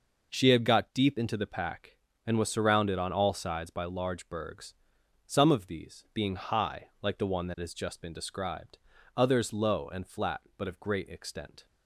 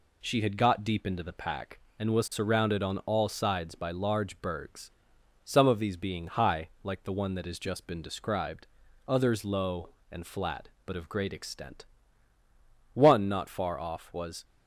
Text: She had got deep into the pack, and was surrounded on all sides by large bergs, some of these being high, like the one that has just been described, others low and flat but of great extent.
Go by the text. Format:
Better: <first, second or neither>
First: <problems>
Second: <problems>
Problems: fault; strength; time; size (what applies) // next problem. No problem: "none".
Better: first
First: none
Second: goes on to say "One not far off was"; from 12.9 s on; 1.5 s long